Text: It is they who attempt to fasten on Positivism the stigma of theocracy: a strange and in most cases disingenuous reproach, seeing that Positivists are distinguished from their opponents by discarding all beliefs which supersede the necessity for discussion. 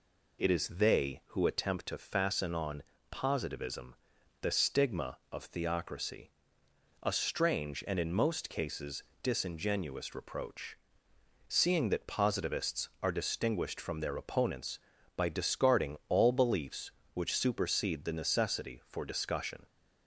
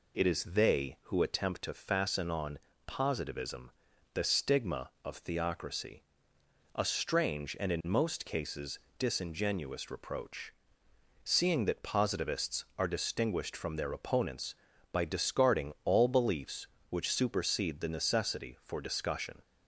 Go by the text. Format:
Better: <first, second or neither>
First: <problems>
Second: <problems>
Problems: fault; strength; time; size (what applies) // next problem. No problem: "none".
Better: neither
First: pauses between "on" and "Positivism"; slight; at 2.8 s; 0.28 s long // pauses between "Positivism" and "the"; noticeable; at 3.9 s; 0.47 s long // pauses between "cases" and "disingenuous"; slight; at 9.0 s; 0.18 s long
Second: pauses between "on" and "Positivism"; slight; at 2.5 s; 0.28 s long // pauses between "Positivism" and "the"; at 3.6 s; 0.44 s long // pauses between "cases" and "disingenuous"; slight; at 8.7 s; 0.18 s long